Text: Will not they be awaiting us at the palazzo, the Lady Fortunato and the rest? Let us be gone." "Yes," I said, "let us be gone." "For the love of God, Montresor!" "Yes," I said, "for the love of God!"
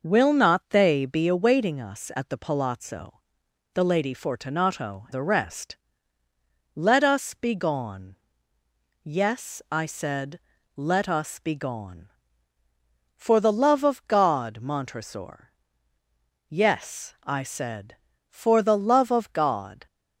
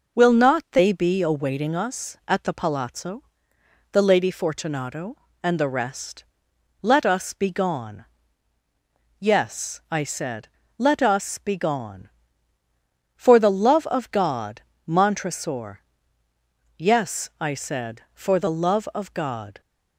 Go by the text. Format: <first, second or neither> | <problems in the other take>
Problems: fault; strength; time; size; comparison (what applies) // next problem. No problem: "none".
second | skips "and"; at 5.0 s